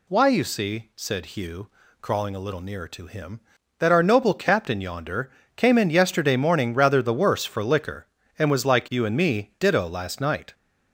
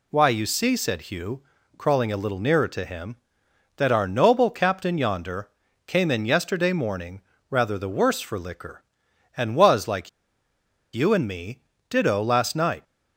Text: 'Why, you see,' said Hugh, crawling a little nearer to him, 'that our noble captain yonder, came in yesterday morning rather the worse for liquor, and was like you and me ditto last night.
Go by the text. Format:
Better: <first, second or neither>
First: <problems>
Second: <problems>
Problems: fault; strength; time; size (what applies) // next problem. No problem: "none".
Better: first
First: none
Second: pauses between "morning" and "rather"; slight; at 7.2 s; 0.28 s long // pauses between "like" and "you"; noticeable; at 10.0 s; 0.85 s long // pauses between "me" and "ditto"; slight; at 11.6 s; 0.26 s long